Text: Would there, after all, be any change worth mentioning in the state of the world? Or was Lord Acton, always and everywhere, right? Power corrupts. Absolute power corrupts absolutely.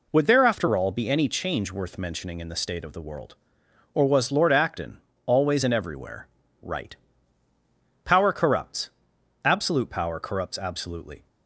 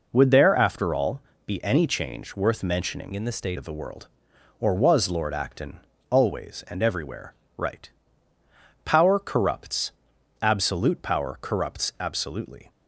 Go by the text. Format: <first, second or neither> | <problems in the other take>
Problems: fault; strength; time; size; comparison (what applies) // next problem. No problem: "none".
first | changes voice from "in" to "state"; from 3.1 to 3.5 s; 0.4 s long